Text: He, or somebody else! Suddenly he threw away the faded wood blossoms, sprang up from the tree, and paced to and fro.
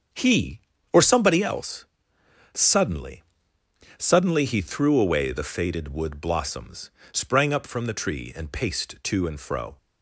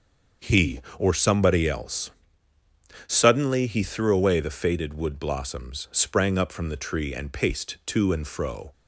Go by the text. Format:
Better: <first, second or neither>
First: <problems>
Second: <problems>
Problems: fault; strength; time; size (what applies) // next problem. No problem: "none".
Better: second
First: starts louder than the rest; until 1.4 s; 7 dB // says "Suddenly" twice; at 3.9 s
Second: starts louder than the rest; until 1.5 s; 6.5 dB